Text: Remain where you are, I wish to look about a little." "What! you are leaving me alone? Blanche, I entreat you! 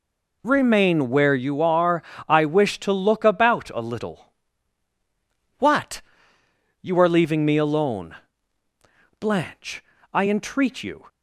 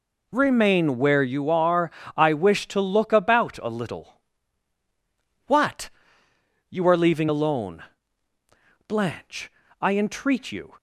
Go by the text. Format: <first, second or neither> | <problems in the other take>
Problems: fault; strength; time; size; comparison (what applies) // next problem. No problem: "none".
first | skips "me"; at 7.2 s